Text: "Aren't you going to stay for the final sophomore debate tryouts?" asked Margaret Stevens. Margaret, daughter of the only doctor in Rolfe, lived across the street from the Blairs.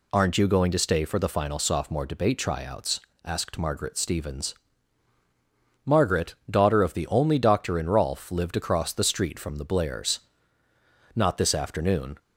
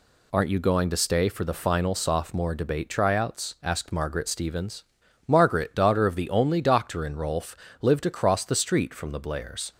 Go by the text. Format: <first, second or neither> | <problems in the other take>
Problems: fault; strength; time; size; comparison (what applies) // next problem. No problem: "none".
second | goes on to say "Not this afternoon"; noticeable; from 11.1 s on; 1.0 s long